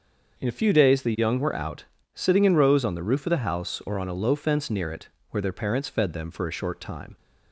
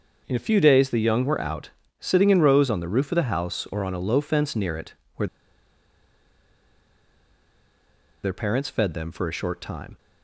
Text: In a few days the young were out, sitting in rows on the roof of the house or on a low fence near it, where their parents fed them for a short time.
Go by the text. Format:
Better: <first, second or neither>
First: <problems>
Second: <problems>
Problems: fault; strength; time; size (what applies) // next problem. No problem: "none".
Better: first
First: starts louder than the rest; until 1.4 s; 6 dB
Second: starts louder than the rest; until 1.2 s; 6 dB // pauses between "where" and "their"; strong; at 5.2 s; 2.9 s long